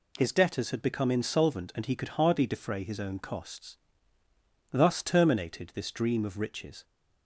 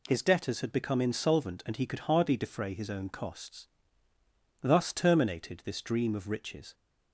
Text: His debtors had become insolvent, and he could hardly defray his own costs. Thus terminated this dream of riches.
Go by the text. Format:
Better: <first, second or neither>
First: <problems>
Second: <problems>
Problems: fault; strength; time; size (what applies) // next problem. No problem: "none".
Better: neither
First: none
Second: none